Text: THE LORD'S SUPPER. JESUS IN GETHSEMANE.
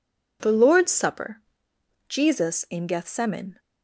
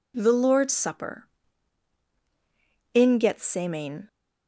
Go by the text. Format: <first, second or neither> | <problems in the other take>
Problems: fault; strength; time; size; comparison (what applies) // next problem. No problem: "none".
first | skips "JESUS"; at 2.1 s